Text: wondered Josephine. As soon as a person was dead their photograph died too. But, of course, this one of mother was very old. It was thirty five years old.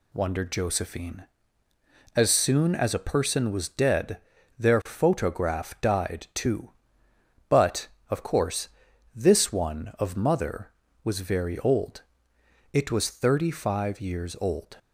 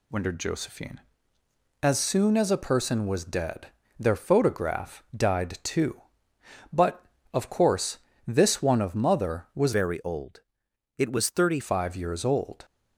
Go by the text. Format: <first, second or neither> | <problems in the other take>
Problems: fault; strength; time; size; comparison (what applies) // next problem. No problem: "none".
first | pauses between "dead" and "their"; slight; at 3.6 s; 0.30 s long; also in the first // changes voice from "very" to "thirty"; from 9.7 to 11.5 s; 1.8 s long